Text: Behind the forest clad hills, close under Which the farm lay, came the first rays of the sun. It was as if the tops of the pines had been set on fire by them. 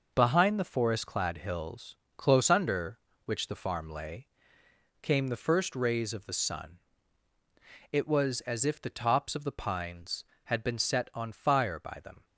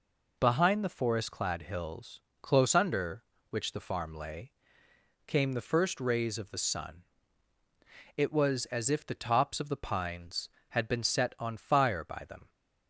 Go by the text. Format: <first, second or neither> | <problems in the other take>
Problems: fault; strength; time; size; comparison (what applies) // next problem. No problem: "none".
second | gets quieter; throughout; 7 dB